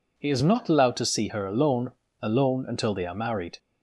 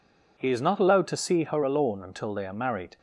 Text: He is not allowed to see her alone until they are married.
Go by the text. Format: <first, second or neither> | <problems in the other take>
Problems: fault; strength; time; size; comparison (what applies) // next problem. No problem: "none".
second | says "alone" twice; at 2.2 s